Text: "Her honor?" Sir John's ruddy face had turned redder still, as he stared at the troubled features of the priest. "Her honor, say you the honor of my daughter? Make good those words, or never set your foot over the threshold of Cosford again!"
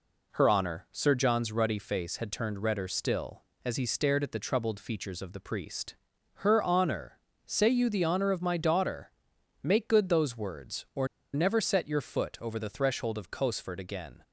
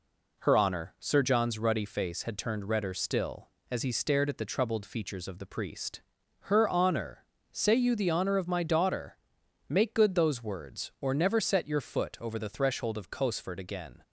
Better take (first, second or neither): second